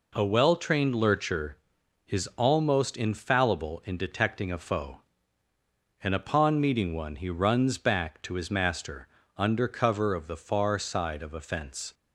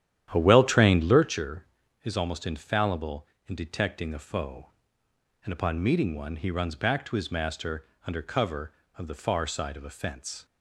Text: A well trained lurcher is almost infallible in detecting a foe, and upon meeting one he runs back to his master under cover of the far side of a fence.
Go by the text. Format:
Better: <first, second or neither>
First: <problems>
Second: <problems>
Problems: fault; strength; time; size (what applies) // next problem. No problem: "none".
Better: first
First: pauses between "master" and "under"; slight; at 9.0 s; 0.28 s long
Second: starts louder than the rest; strong; until 1.5 s; 10.5 dB // pauses between "master" and "under"; slight; at 7.8 s; 0.18 s long